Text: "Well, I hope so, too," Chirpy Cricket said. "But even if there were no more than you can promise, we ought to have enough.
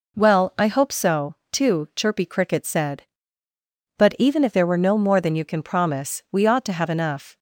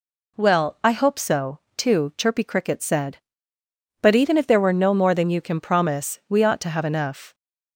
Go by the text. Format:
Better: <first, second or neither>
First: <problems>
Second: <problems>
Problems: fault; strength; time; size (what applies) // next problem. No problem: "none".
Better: neither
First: none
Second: none